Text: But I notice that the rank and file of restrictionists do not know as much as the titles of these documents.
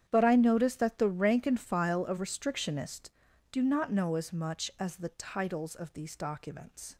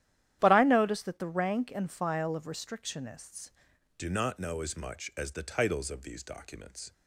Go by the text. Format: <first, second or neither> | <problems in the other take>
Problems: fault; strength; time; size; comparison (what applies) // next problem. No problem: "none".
first | starts louder than the rest; strong; until 1.4 s; 11.5 dB; strong in the first // changes voice at "do"; from 3.9 s on; 3.0 s long